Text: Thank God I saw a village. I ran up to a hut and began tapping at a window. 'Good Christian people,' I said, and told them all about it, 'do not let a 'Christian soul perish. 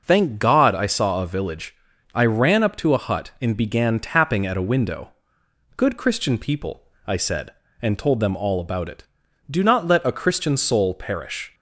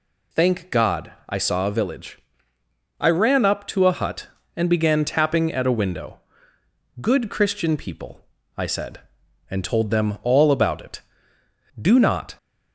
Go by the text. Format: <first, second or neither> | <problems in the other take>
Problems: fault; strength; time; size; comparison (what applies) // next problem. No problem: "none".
first | pauses between "God" and "I"; slight; at 1.1 s; 0.16 s long // stops before "let a Christian soul perish"; at 12.3 s